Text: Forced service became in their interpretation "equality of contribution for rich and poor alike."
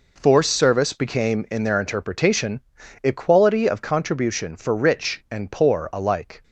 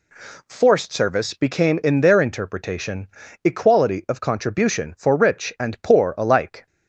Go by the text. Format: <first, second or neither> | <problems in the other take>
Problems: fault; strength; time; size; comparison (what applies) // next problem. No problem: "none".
neither | pauses between "interpretation" and "equality"; the same in both